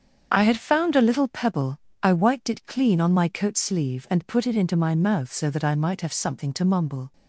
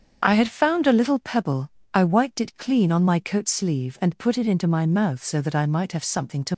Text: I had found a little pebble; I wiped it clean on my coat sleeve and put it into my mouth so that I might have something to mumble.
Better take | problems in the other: first | starts louder than the rest; strong; until 1.2 s; 7 dB; strong in the first // stops before "mumble"; at 6.5 s

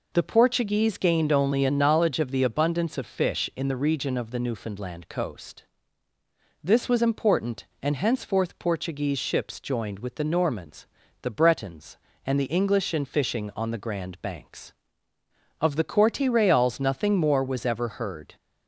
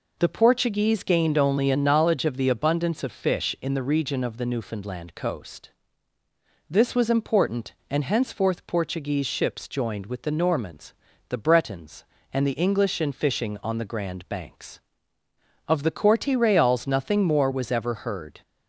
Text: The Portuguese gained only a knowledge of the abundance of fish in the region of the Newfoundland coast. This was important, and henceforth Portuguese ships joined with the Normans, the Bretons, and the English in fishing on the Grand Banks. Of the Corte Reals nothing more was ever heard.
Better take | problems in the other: neither | none

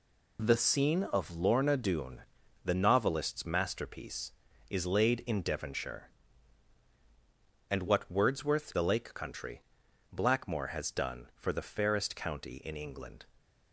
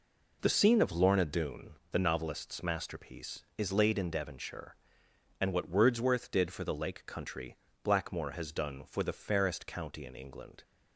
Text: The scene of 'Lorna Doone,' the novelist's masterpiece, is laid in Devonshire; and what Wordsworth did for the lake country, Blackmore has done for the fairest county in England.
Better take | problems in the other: second | skips "did for"; at 8.7 s

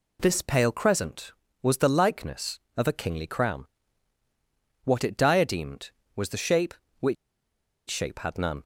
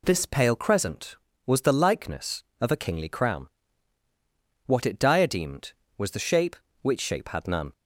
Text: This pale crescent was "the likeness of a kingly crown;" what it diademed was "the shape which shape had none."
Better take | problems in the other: second | pauses between "which" and "shape"; noticeable; at 7.1 s; 0.73 s long

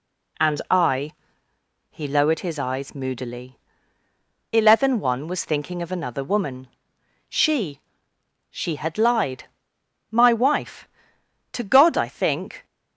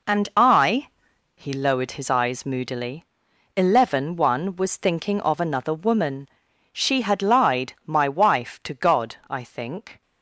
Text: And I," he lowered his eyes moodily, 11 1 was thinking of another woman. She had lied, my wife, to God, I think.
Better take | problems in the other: second | says "She" twice; at 8.5 s

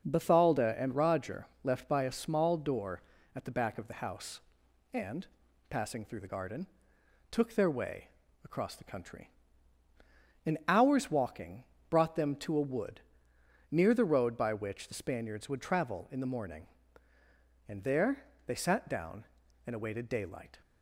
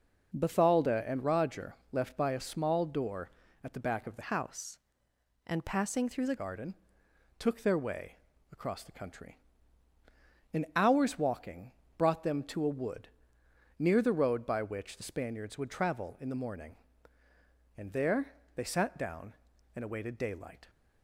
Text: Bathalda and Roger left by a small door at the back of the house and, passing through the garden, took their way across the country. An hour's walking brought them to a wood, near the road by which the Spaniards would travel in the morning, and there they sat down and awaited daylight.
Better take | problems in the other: first | pauses between "Roger" and "left"; slight; at 1.7 s; 0.16 s long; slight in the first // changes voice from "house" to "the"; from 4.2 to 6.3 s; 2.1 s long // pauses between "way" and "across"; slight; at 8.1 s; 0.36 s long; slight in the first // pauses between "walking" and "brought"; slight; at 11.7 s; 0.24 s long; slight in the first // pauses between "there" and "they"; slight; at 18.3 s; 0.22 s long; slight in the first

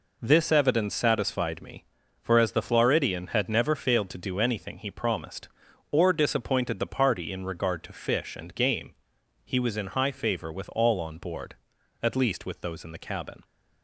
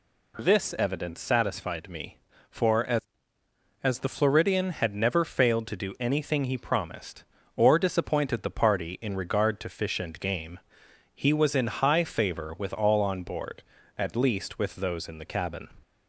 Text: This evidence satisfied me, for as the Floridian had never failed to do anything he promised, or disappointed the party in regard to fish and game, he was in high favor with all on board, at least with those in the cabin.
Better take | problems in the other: first | says "as" twice; at 3.8 s

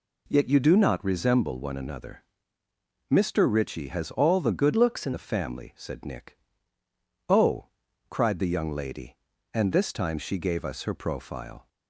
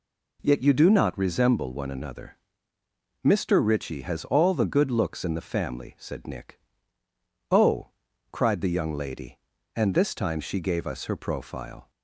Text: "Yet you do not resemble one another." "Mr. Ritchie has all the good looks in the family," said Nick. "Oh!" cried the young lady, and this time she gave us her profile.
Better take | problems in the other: second | changes voice from "looks" to "in"; from 4.7 to 5.1 s; 0.4 s long

